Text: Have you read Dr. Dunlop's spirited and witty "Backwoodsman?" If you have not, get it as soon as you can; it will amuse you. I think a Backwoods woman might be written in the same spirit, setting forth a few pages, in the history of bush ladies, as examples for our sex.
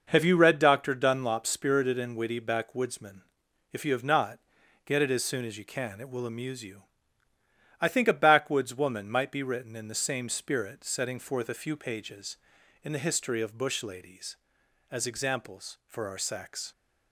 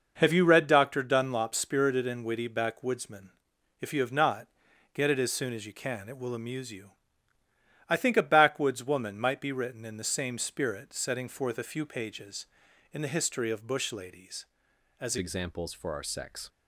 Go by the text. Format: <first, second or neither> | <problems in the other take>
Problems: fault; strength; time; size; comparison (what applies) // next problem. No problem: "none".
first | changes voice at "examples"; from 15.1 s on; 1.3 s long